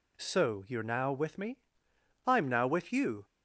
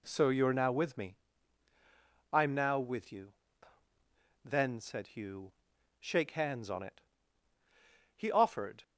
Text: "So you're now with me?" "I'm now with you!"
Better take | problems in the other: first | goes on to say "Then said Hugh shake hands on it He offered"; strong; from 4.4 s on; 4.3 s long

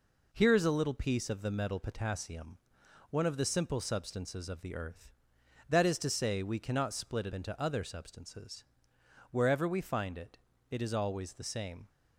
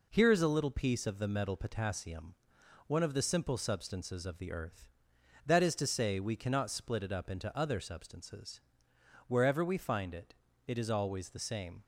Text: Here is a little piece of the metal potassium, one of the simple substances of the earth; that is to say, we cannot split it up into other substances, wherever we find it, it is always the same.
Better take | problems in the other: second | skips "up"; at 7.3 s

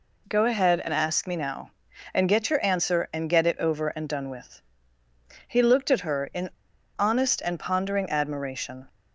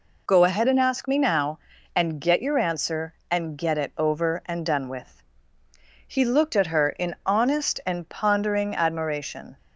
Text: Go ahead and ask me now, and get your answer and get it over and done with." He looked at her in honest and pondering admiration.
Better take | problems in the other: second | pauses between "in" and "honest"; noticeable; at 6.4 s; 0.49 s long

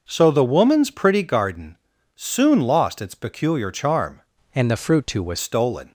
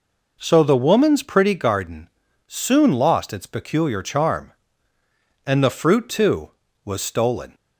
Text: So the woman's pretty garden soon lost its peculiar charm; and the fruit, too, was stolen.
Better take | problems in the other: second | pauses between "garden" and "soon"; at 1.7 s; 0.38 s long; also in the second // changes voice from "and" to "was"; from 4.5 to 5.3 s; 0.8 s long

